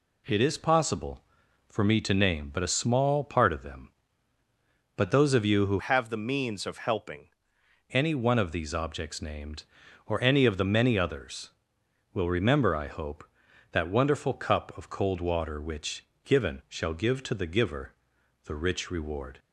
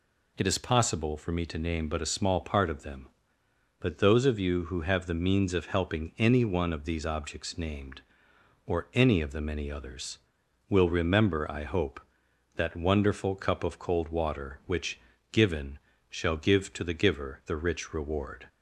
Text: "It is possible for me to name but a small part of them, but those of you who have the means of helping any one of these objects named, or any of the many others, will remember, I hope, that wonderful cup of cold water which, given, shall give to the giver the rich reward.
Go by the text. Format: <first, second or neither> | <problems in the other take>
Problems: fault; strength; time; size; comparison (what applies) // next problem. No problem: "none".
second | changes voice from "have" to "helping"; from 5.7 to 7.2 s; 1.5 s long // pauses between "giver" and "the"; noticeable; at 17.9 s; 0.50 s long